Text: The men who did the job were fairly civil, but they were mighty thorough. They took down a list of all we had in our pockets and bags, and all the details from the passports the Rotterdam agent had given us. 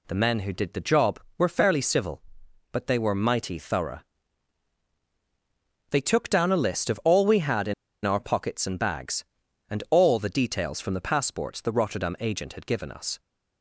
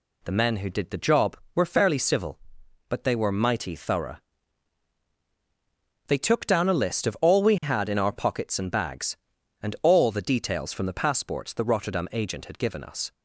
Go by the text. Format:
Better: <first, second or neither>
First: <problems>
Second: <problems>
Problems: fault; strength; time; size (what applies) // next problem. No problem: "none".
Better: second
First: pauses between "in" and "our"; slight; at 7.7 s; 0.31 s long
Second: none